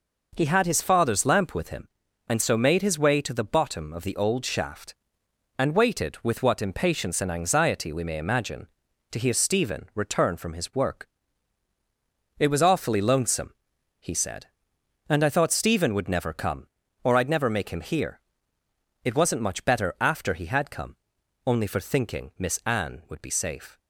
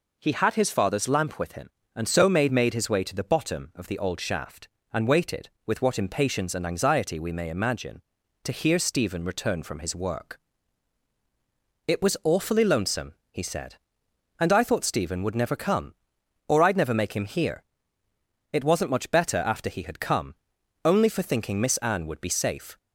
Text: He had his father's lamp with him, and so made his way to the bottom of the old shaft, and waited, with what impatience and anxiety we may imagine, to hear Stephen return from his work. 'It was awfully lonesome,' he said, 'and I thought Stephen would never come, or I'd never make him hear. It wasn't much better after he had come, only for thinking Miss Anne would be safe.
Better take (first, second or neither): first